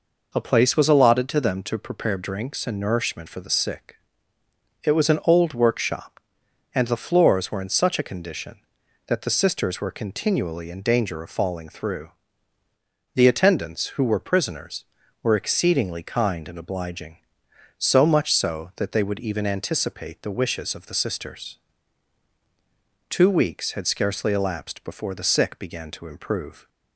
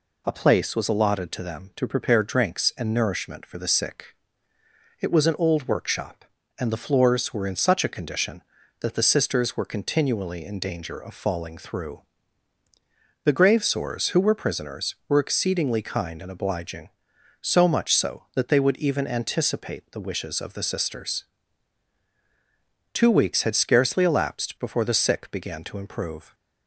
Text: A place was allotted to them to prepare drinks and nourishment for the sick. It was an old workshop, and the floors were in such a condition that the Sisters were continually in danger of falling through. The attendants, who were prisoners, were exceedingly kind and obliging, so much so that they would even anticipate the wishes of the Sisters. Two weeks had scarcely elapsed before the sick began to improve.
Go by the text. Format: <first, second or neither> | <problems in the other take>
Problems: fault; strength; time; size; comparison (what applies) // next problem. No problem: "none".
first | says "gravesores" for "attendants"; at 13.3 s